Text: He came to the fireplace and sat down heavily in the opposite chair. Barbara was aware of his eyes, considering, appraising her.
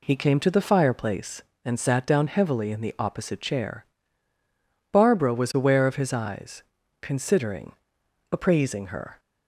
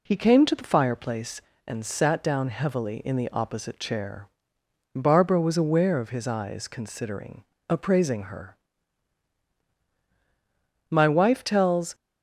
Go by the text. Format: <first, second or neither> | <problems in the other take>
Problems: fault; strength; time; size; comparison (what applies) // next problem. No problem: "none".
first | goes on to say "My wife tells"; noticeable; from 10.9 s on; 1.0 s long